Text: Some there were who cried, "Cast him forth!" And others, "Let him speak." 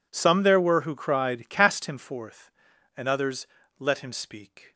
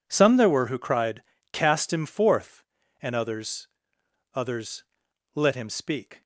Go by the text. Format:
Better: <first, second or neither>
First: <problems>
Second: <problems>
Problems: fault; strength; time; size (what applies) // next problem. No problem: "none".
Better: first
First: none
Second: says "others" twice; at 4.3 s